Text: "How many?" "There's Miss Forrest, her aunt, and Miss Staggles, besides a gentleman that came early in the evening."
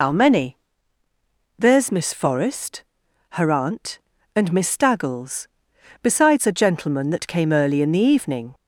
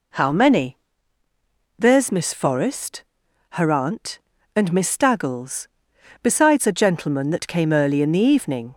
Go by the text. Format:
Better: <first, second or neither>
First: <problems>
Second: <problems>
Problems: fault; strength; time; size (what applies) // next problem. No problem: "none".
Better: second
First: loses the start of "How"; at 0.0 s; 75 ms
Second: none